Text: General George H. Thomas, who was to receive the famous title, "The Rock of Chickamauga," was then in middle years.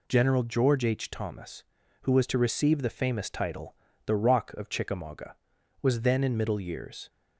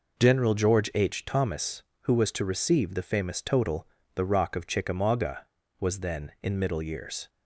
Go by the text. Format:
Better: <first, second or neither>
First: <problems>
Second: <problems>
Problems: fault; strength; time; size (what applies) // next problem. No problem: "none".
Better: first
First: none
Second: says "total" for "title"; at 3.3 s